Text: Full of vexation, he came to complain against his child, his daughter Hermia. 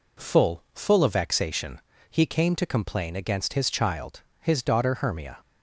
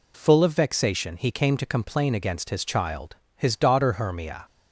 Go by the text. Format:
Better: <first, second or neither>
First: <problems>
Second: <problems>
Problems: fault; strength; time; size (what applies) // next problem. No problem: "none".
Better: second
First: says "Full" twice; at 0.7 s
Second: none